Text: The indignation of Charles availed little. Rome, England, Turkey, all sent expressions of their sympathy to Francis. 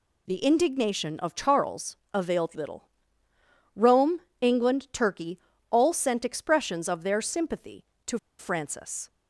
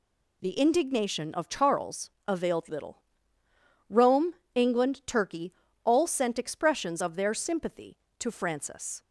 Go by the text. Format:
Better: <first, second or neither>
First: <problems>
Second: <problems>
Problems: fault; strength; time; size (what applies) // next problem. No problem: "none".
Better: second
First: pauses between "Charles" and "availed"; slight; at 1.9 s; 0.16 s long // pauses between "to" and "Francis"; slight; at 8.1 s; 0.21 s long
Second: pauses between "Charles" and "availed"; slight; at 2.1 s; 0.16 s long